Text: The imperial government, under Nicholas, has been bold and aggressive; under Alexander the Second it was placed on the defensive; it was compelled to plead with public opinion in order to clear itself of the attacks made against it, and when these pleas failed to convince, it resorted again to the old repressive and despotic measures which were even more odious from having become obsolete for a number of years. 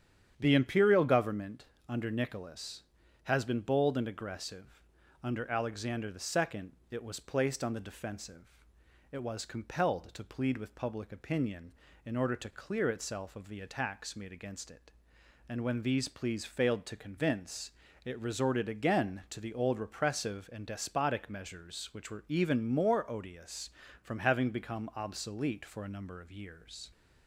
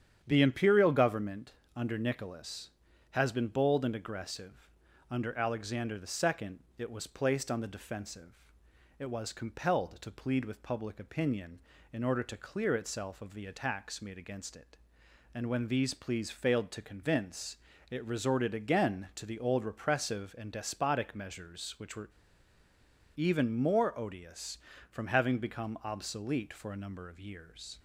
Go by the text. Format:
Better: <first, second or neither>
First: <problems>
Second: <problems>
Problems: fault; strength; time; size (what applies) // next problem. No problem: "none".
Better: first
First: starts louder than the rest; strong; until 1.3 s; 9 dB // pauses between "Second" and "it"; slight; at 6.7 s; 0.18 s long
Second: starts louder than the rest; strong; until 1.2 s; 9 dB // pauses between "Second" and "it"; slight; at 6.6 s; 0.18 s long // pauses between "were" and "even"; at 22.1 s; 1.0 s long